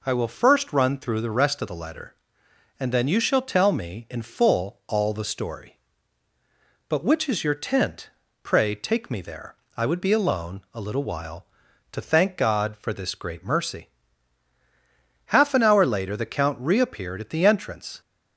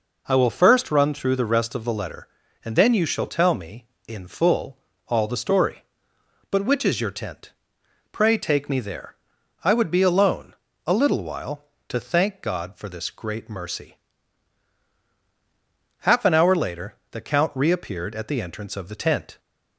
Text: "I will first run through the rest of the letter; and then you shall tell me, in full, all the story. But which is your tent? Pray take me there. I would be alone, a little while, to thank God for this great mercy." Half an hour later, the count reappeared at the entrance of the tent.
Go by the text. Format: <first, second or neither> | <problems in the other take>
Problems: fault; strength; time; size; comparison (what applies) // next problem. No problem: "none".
second | stops before "of the tent"; at 18.0 s